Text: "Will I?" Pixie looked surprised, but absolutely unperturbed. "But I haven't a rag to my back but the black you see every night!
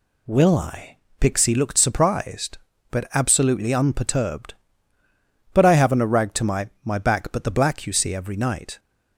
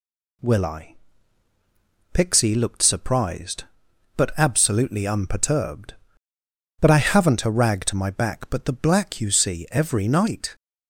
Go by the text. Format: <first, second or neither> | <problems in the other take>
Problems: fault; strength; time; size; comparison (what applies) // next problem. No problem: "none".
second | says "my" twice; at 6.8 s